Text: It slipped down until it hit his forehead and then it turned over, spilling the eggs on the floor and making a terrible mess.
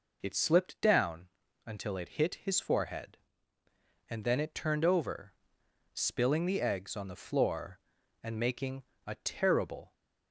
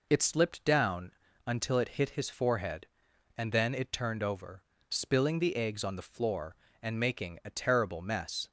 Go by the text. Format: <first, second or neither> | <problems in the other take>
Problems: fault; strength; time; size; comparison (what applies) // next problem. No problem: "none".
second | pauses between "down" and "until"; slight; at 1.2 s; 0.36 s long; slight in the second // pauses between "making" and "a"; slight; at 8.8 s; 0.24 s long // stops before "mess"; at 9.9 s